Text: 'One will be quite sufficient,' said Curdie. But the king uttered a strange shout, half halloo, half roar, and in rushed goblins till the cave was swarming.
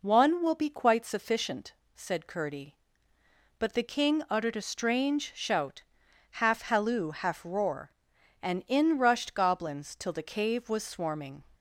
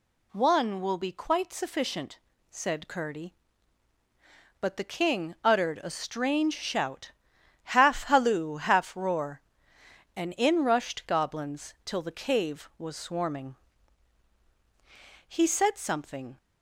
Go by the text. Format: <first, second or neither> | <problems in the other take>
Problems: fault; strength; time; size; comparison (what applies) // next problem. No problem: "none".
first | goes on to say "He said something"; noticeable; from 15.2 s on; 1.1 s long